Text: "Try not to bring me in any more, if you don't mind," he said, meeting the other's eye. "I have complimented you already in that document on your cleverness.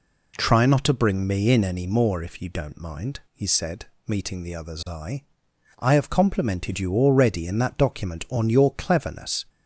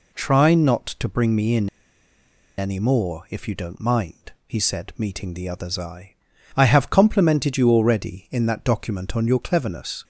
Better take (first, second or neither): first